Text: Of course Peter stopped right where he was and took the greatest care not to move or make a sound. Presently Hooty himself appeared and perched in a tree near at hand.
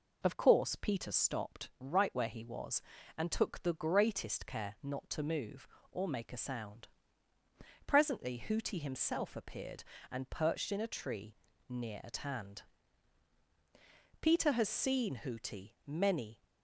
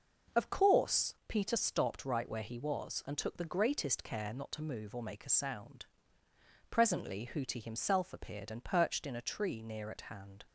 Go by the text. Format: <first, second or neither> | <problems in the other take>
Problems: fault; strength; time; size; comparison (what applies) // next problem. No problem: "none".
second | pauses between "tree" and "near"; slight; at 11.3 s; 0.34 s long // goes on to say "Peter has seen Hooty many"; strong; from 14.2 s on; 2.2 s long